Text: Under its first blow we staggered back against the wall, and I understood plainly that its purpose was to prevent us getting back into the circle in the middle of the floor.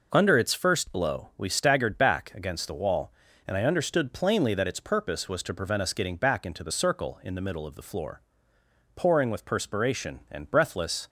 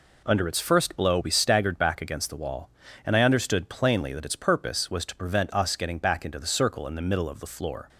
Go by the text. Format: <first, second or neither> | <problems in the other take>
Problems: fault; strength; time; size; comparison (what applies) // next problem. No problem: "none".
second | goes on to say "Pouring with perspiration and breathless"; strong; from 8.9 s on; 2.1 s long